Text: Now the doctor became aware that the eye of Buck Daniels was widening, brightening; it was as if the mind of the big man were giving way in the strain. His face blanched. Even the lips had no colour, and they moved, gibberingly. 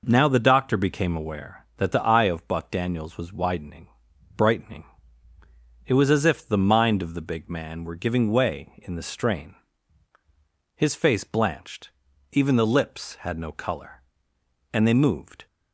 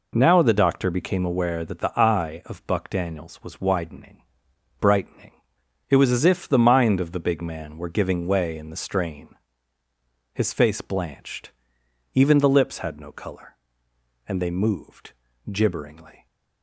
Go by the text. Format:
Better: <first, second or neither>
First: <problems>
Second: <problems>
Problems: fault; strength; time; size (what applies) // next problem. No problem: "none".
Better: second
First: stops before "gibberingly"; at 15.4 s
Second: none